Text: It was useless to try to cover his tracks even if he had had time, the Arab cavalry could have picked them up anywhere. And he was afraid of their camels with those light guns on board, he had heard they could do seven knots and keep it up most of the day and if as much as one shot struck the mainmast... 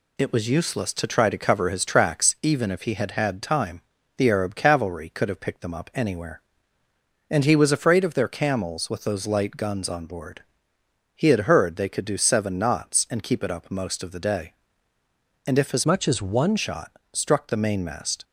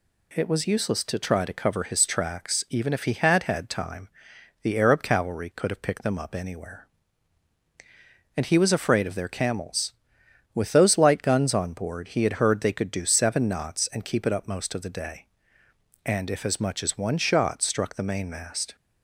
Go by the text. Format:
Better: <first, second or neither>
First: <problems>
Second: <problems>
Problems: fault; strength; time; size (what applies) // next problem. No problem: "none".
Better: second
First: changes voice from "much" to "one"; from 15.8 to 16.5 s; 0.7 s long // pauses between "shot" and "struck"; slight; at 16.9 s; 0.22 s long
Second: none